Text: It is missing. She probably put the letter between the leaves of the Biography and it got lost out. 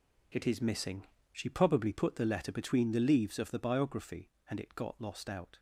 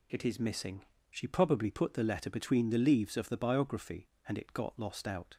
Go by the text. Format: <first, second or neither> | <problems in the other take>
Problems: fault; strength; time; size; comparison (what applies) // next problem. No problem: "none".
second | gets quieter; strong; throughout; 11 dB